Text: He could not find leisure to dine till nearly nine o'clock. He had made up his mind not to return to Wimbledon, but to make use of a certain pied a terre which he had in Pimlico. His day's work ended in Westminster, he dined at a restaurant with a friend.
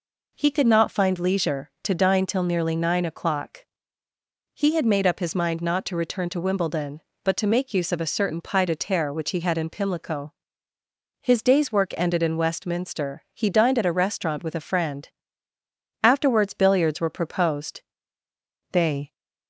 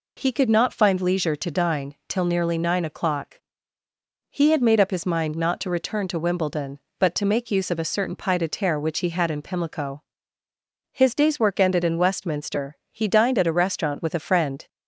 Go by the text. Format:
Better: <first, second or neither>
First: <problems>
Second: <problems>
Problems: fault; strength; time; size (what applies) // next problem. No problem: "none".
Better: second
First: goes on to say "Afterwards billiards were proposed They"; strong; from 16.0 s on; 3.1 s long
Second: none